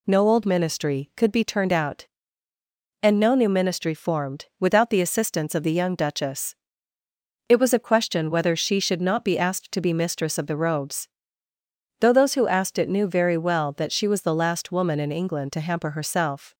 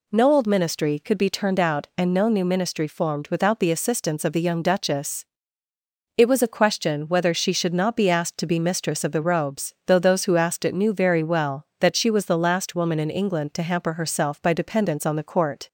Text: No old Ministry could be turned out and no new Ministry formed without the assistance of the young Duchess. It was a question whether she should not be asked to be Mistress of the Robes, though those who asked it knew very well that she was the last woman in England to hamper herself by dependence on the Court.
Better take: second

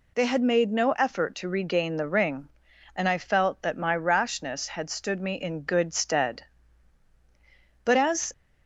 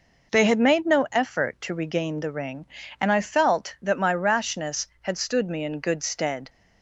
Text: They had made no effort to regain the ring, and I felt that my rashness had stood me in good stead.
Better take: second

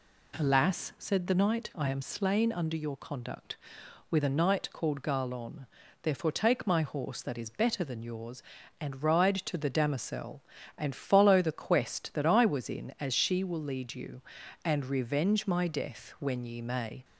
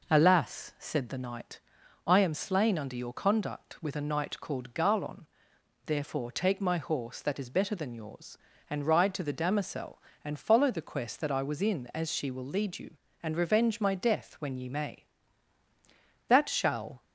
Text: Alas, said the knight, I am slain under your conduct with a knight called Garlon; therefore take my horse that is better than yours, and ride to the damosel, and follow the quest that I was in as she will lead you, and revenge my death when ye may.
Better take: first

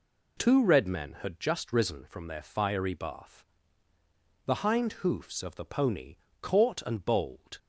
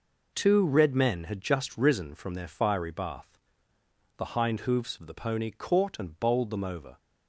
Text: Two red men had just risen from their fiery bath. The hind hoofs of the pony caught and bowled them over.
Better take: second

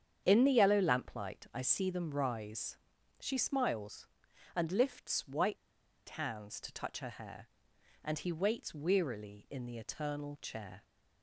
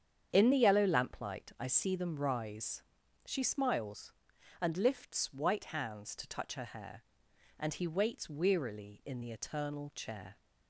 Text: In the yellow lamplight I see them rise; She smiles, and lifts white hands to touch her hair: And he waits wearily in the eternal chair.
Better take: second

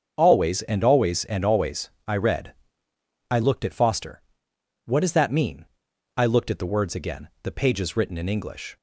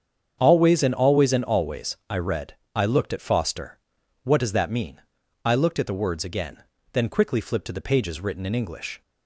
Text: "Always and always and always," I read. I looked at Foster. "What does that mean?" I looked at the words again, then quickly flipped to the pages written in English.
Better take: second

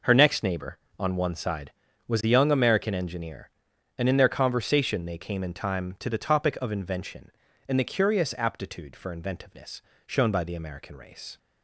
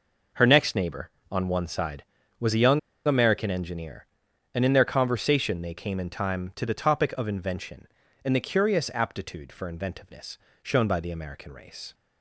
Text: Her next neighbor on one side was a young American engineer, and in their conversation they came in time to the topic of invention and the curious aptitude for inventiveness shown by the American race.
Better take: first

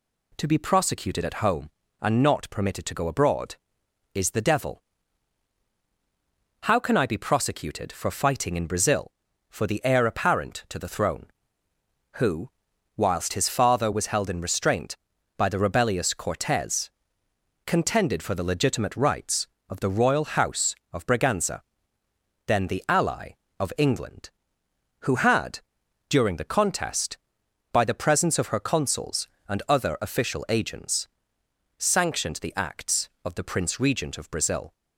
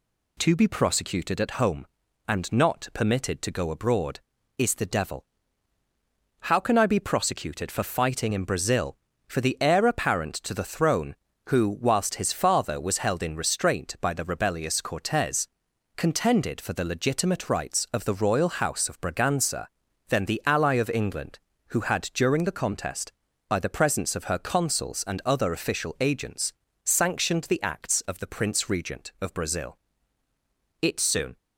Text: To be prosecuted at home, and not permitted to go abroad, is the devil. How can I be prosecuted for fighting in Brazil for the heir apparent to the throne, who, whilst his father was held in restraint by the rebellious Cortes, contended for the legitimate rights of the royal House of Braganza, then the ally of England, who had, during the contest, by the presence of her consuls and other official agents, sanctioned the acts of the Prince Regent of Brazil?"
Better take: first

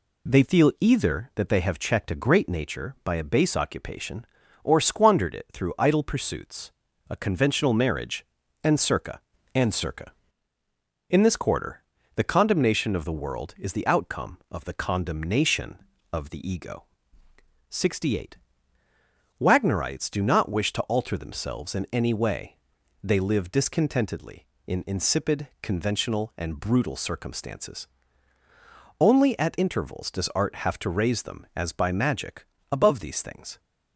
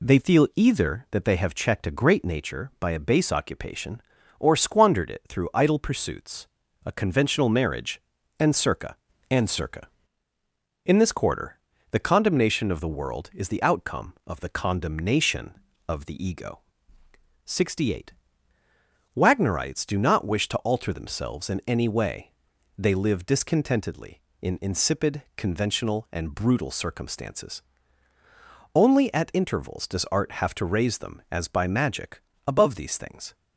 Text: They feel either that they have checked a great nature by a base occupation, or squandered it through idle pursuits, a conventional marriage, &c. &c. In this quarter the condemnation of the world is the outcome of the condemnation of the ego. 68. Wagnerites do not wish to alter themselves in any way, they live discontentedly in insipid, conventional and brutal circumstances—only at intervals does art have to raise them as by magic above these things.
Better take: neither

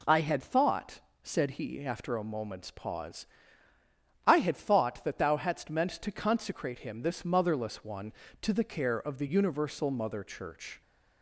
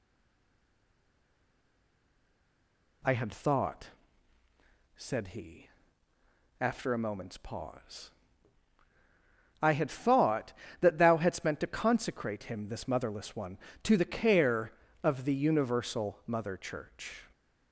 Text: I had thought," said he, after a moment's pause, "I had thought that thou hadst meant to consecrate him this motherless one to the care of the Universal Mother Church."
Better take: first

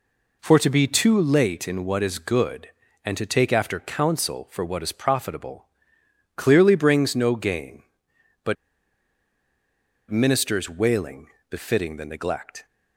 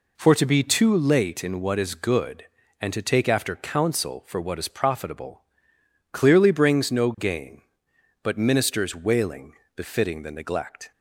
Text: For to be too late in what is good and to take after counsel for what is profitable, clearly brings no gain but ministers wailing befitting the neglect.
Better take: second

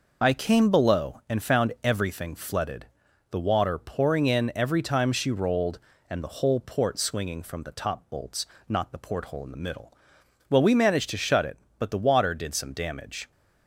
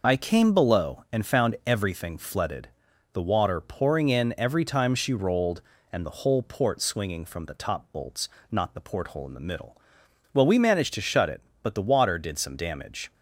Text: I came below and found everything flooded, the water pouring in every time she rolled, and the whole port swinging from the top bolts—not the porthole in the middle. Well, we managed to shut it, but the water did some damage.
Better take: neither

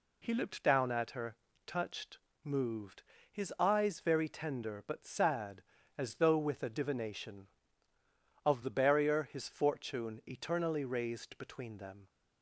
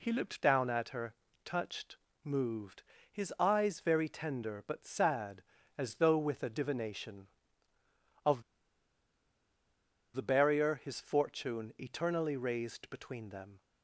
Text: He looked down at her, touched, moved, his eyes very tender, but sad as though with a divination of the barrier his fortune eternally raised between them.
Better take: first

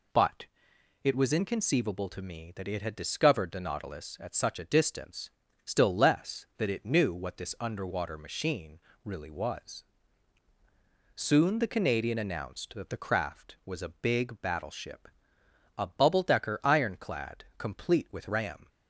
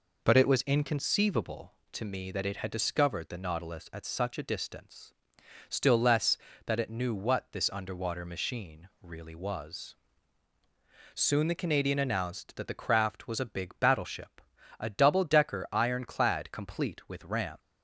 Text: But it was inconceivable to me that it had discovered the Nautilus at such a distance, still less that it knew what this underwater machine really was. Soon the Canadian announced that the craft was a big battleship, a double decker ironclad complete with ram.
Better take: second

